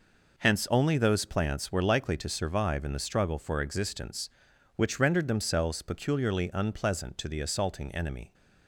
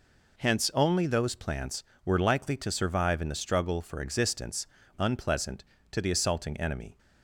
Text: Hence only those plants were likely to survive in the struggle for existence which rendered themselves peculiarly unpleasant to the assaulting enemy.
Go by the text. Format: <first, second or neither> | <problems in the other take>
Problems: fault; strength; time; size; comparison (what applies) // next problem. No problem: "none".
first | skips "which rendered themselves peculiarly"; at 4.8 s